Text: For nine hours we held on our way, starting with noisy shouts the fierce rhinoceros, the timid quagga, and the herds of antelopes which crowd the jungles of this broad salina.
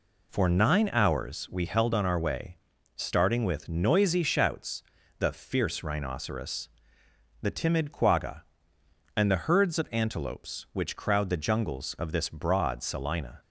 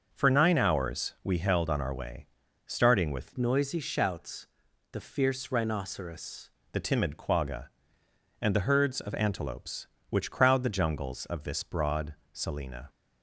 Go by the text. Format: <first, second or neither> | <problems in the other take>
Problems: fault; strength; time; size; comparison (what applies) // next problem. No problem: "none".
first | starts louder than the rest; noticeable; until 1.1 s; 6 dB // changes voice from "noisy" to "rhinoceros"; from 3.3 to 6.4 s; 3.1 s long // pauses between "shouts" and "the"; at 4.4 s; 0.44 s long; slight in the first // pauses between "broad" and "salina"; slight; at 12.1 s; 0.20 s long